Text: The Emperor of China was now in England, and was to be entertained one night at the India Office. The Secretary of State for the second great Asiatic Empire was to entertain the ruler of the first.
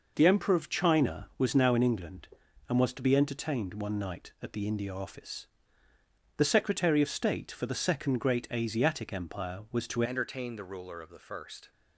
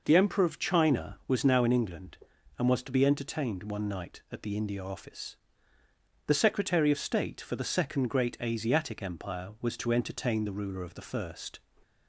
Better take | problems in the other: second | changes voice at "entertain"; from 10.0 s on; 1.7 s long

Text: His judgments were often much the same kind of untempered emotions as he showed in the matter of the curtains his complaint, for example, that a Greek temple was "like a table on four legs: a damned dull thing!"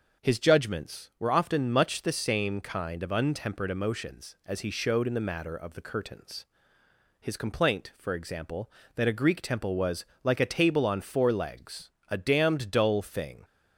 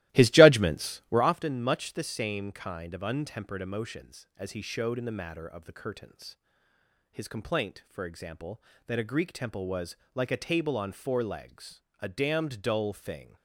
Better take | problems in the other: first | starts louder than the rest; strong; until 1.3 s; 16.5 dB // pauses between "curtains" and "his"; noticeable; at 6.3 s; 0.76 s long; noticeable in the first // pauses between "was" and "like"; slight; at 9.9 s; 0.18 s long; slight in the first

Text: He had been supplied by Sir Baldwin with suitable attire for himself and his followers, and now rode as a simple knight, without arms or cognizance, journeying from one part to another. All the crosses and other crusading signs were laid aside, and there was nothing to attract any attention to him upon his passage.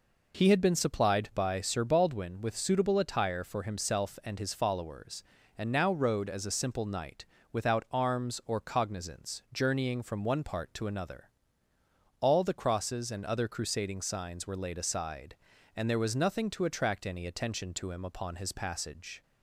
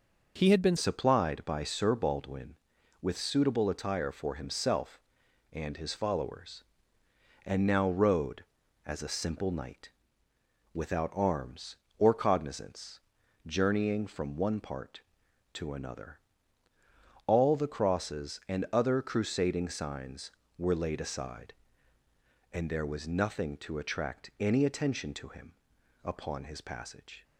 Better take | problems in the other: first | changes voice at "supplied"; from 0.7 s on; 26.5 s long // pauses between "him" and "upon"; noticeable; at 25.5 s; 0.50 s long

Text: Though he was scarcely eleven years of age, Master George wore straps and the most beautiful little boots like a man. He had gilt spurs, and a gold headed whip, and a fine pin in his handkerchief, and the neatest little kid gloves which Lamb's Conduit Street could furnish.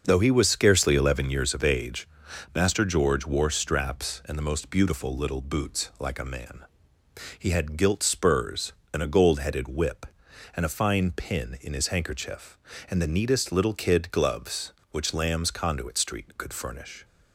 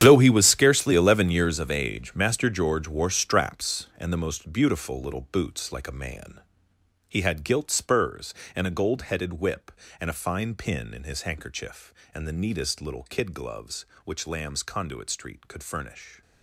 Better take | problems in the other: first | gets quieter; strong; throughout; 14 dB // starts louder than the rest; strong; until 1.0 s; 9.5 dB; also in the first

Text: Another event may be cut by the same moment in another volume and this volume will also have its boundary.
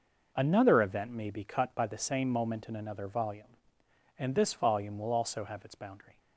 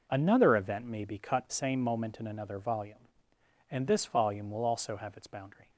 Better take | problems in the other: first | skips "by the"; at 1.4 s

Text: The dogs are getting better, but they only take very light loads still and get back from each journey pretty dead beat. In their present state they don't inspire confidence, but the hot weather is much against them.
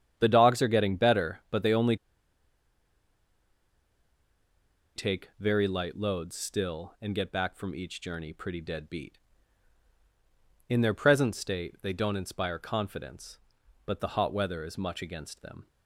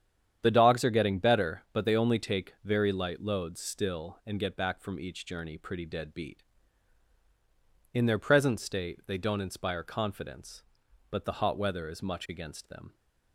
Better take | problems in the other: second | starts louder than the rest; strong; until 1.1 s; 9 dB; strong in the second // pauses between "only" and "take"; strong; at 1.9 s; 3.0 s long

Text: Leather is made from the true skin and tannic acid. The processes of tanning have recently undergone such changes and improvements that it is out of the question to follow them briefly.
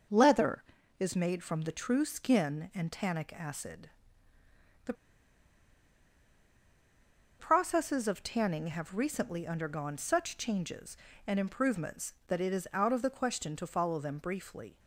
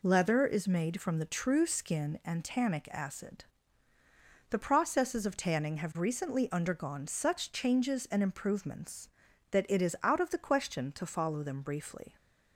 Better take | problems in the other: second | pauses between "The" and "processes"; strong; at 4.9 s; 2.4 s long

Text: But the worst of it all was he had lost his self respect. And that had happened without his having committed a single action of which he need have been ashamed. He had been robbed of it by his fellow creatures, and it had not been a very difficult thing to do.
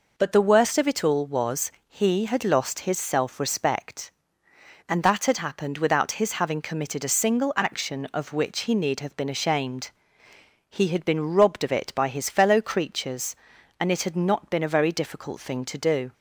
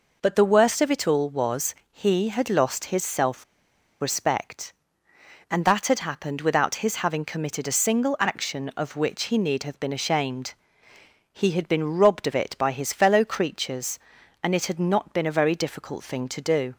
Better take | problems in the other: first | pauses between "was" and "he"; slight; at 1.7 s; 0.18 s long; slight in the first // pauses between "self" and "respect"; noticeable; at 3.4 s; 0.58 s long

